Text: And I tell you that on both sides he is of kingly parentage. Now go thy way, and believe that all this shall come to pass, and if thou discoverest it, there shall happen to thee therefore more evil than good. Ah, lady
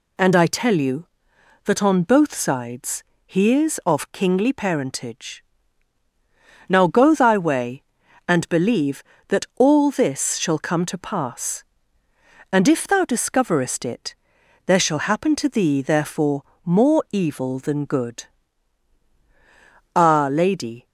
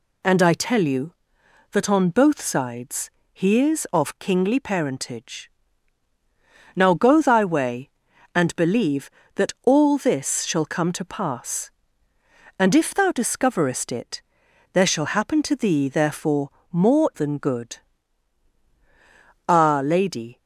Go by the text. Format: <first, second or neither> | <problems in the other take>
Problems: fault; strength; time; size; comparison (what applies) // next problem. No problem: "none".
first | pauses between "sides" and "he"; slight; at 3.1 s; 0.22 s long; slight in the first // pauses between "therefore" and "more"; slight; at 16.4 s; 0.22 s long; slight in the first // skips "evil"; at 17.1 s